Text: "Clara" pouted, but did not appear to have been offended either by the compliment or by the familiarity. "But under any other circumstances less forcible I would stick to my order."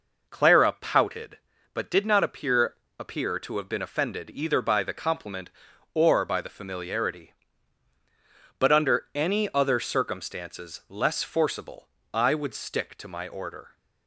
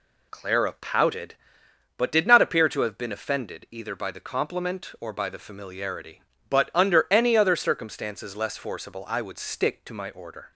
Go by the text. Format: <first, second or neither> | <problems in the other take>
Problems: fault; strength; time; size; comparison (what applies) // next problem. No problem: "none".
second | says "appear" twice; at 2.9 s // pauses between "forcible" and "I"; slight; at 11.8 s; 0.26 s long